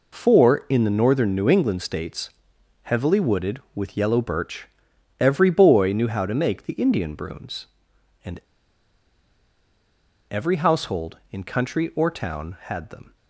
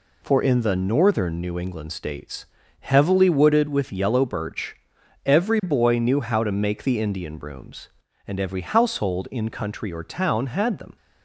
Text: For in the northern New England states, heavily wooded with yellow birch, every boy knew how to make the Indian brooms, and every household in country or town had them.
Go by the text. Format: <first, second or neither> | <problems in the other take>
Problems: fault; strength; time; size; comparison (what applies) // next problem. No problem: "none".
second | pauses between "and" and "every"; strong; at 8.3 s; 1.8 s long